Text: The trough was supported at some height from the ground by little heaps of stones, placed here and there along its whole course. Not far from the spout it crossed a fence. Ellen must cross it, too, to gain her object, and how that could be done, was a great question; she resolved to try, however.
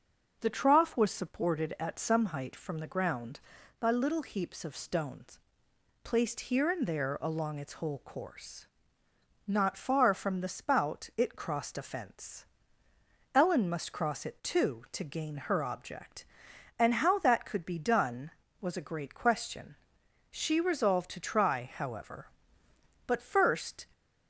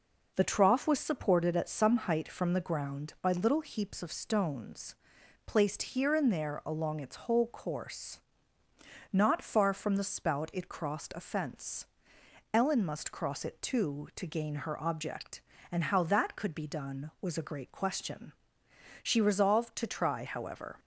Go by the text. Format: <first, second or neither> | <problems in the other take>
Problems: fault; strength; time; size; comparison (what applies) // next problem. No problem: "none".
second | goes on to say "But first"; noticeable; from 23.0 s on; 0.80 s long